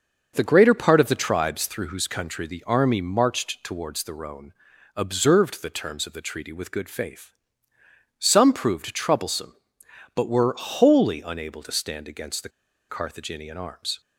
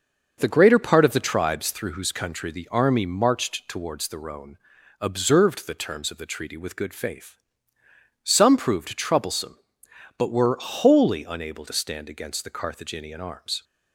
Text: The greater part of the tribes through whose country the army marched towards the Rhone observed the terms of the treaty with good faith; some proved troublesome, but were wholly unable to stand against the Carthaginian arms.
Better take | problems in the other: second | starts louder than the rest; until 1.3 s; 6.5 dB; also in the second // pauses between "Rhone" and "observed"; at 4.5 s; 0.44 s long; also in the second // pauses between "the" and "Carthaginian"; at 12.4 s; 0.40 s long

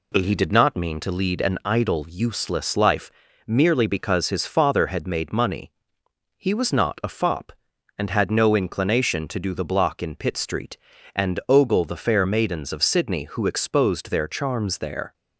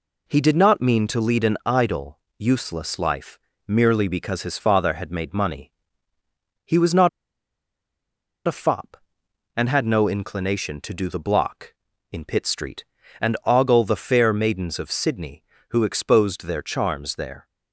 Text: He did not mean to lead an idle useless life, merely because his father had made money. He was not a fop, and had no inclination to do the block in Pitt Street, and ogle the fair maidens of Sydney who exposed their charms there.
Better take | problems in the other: first | pauses between "idle" and "useless"; slight; at 2.1 s; 0.20 s long // pauses between "not" and "a"; strong; at 7.0 s; 1.3 s long

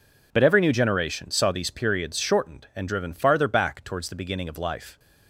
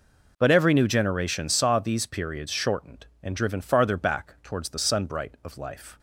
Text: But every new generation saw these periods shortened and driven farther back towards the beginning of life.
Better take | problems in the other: first | says "sunbright" for "beginning"; at 4.7 s

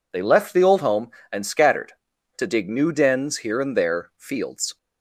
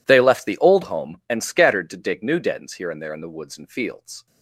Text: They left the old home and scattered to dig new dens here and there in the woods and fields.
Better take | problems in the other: second | skips "in the woods and"; at 4.1 s

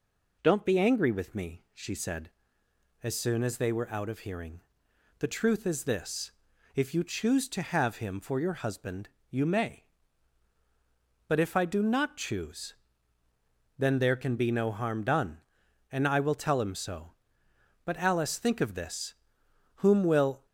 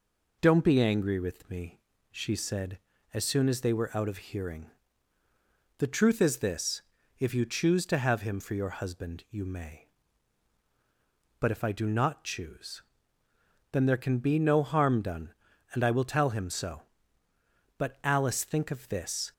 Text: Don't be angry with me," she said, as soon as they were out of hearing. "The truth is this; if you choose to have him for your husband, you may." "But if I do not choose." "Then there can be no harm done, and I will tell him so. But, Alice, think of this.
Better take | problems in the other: second | goes on to say "Whom will"; noticeable; from 19.7 s on; 0.68 s long

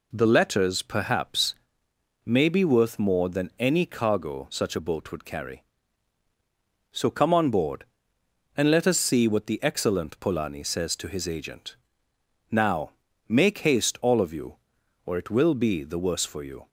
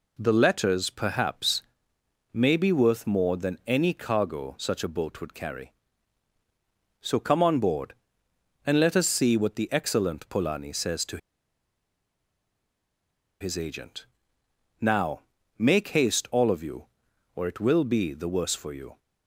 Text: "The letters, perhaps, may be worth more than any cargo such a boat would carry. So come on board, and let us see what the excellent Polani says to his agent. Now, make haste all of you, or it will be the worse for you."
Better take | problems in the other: first | pauses between "to" and "his"; strong; at 11.1 s; 2.2 s long

